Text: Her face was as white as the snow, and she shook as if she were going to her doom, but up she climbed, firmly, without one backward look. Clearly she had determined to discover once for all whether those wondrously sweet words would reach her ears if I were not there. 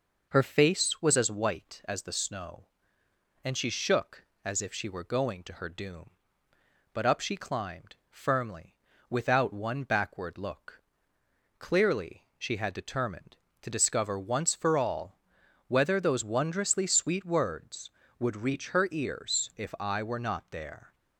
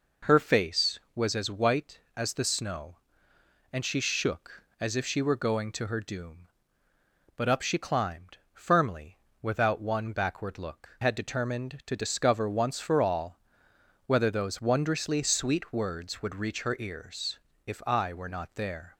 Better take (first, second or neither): first